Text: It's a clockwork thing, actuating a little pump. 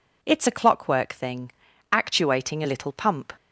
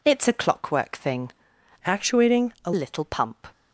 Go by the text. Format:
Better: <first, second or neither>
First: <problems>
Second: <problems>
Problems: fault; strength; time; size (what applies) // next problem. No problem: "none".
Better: first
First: none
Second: changes voice from "actuating" to "a"; from 1.8 to 2.7 s; 0.9 s long